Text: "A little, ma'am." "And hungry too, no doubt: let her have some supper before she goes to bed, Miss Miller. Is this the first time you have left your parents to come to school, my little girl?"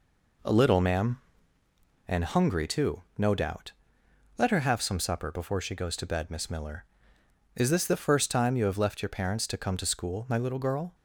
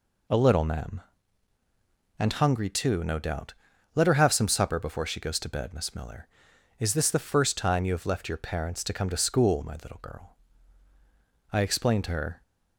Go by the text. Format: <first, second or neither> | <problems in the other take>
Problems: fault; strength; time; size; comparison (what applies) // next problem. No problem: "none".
first | goes on to say "I explained to her"; noticeable; from 11.4 s on; 0.92 s long